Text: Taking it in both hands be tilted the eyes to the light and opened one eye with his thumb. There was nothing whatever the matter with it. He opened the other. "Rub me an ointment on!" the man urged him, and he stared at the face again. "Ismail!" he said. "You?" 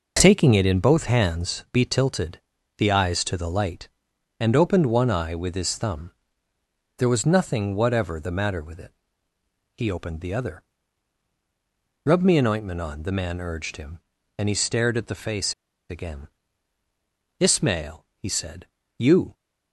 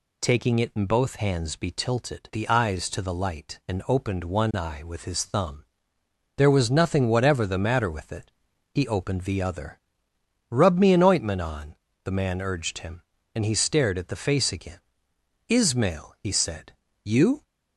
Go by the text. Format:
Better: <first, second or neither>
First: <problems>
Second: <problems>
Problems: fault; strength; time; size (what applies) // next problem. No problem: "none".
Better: second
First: pauses between "tilted" and "the"; at 2.3 s; 0.40 s long // pauses between "face" and "again"; slight; at 15.5 s; 0.35 s long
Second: none